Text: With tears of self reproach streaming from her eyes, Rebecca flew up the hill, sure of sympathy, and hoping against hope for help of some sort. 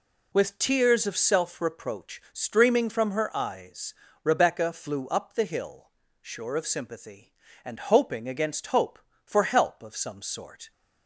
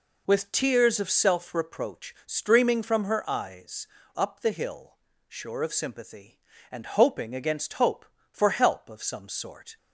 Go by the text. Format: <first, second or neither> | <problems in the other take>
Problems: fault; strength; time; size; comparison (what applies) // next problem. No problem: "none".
first | skips "Rebecca flew"; at 3.9 s